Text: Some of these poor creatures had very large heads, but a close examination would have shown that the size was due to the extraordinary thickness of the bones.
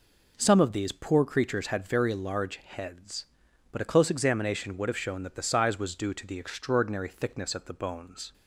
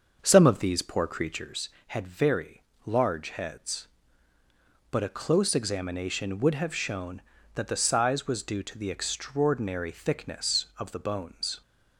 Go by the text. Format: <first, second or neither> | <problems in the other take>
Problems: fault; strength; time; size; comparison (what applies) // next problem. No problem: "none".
first | starts louder than the rest; until 1.5 s; 6.5 dB // pauses between "very" and "large"; slight; at 2.6 s; 0.24 s long